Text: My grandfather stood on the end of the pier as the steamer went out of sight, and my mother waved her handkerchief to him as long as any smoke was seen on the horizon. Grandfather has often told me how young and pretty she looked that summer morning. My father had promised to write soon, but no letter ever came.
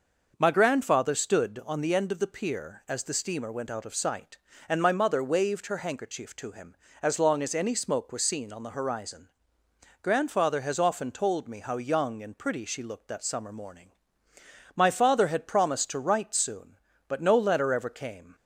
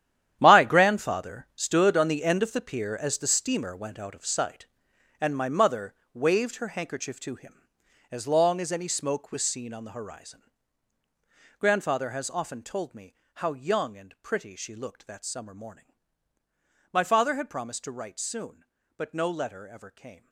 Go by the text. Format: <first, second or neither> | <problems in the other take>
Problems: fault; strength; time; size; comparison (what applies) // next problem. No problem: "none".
first | gets quieter; strong; throughout; 13.5 dB // starts louder than the rest; strong; until 1.4 s; 10.5 dB; noticeable in the first // pauses between "mother" and "waved"; slight; at 5.9 s; 0.18 s long // pauses between "me" and "how"; slight; at 13.1 s; 0.20 s long